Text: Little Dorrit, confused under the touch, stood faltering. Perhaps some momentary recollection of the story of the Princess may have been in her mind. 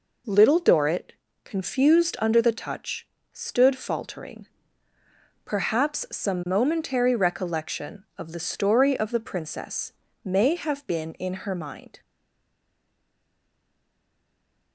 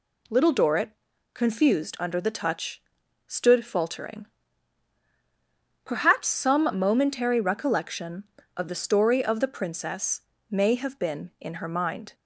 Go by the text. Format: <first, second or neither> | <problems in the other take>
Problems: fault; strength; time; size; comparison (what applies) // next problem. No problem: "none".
second | pauses between "Princess" and "may"; slight; at 9.9 s; 0.32 s long; slight in the second // stays silent after the last word; strong; from 12.0 s on; 2.7 s long